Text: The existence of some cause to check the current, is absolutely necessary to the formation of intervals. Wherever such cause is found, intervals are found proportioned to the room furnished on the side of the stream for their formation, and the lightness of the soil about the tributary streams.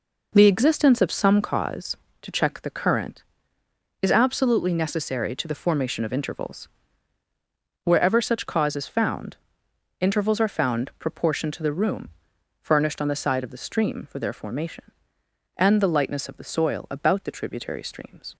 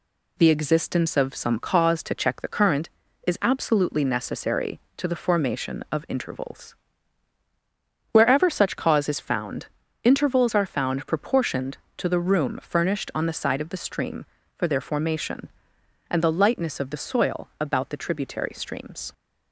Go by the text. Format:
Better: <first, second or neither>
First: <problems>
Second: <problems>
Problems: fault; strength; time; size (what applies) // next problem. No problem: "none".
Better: second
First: starts louder than the rest; noticeable; until 1.5 s; 4.5 dB // pauses between "room" and "furnished"; noticeable; at 12.0 s; 0.52 s long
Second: none